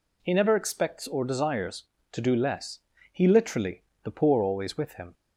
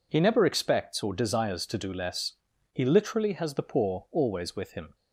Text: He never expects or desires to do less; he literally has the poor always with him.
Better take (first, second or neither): second